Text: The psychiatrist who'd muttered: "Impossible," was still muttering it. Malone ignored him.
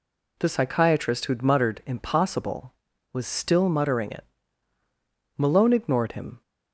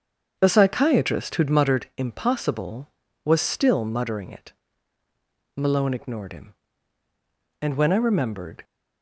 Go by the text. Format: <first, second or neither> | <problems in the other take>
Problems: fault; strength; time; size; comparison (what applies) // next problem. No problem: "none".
first | starts louder than the rest; strong; until 1.4 s; 7 dB // goes on to say "And when I remembered"; noticeable; from 7.5 s on; 1.0 s long